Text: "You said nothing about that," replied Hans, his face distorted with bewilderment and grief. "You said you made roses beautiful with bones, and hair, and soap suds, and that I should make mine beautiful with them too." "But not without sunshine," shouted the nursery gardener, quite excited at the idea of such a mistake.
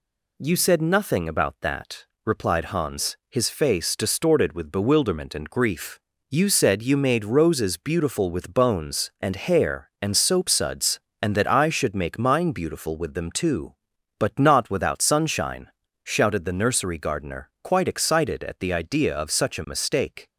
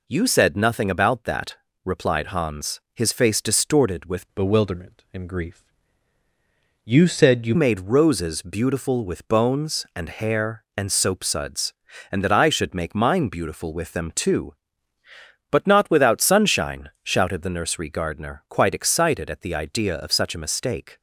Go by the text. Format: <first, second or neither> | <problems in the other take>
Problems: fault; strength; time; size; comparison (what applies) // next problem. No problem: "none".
first | changes voice from "bewilderment" to "you"; from 4.3 to 7.5 s; 3.2 s long